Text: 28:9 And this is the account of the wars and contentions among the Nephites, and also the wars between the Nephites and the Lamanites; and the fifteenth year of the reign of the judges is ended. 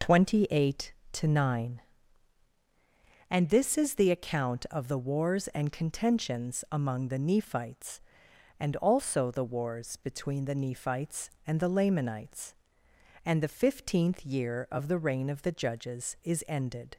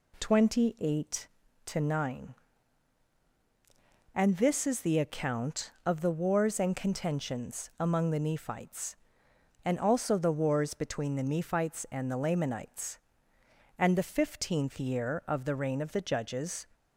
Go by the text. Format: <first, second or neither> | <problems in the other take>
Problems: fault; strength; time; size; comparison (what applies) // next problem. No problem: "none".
first | stops before "is ended"; at 16.7 s